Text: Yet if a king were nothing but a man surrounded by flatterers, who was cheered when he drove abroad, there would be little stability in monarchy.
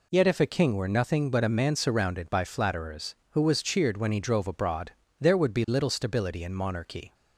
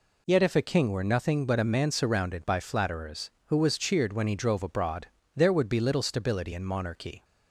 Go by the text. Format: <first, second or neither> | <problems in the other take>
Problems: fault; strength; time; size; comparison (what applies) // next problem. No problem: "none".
neither | none